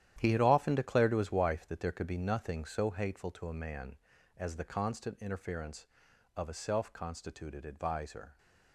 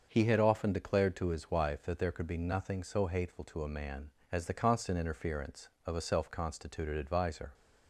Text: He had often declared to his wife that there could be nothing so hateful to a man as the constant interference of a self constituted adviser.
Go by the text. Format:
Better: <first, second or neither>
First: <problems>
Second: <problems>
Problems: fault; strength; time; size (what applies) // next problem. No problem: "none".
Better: second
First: gets quieter; strong; throughout; 11 dB // starts louder than the rest; strong; until 1.1 s; 11 dB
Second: starts louder than the rest; until 1.1 s; 6.5 dB